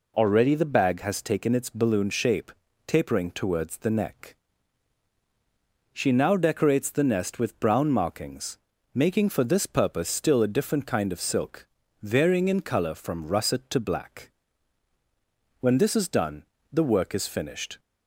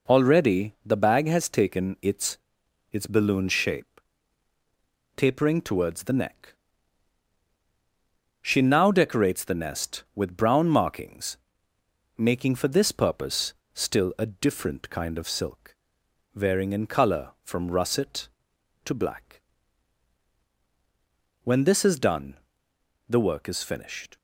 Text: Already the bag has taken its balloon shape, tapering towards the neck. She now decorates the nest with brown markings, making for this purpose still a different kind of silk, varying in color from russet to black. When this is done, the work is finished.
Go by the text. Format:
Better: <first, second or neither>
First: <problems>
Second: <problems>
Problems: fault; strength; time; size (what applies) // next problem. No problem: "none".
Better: first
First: none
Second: says "its" twice; at 2.9 s // pauses between "purpose" and "still"; slight; at 13.5 s; 0.22 s long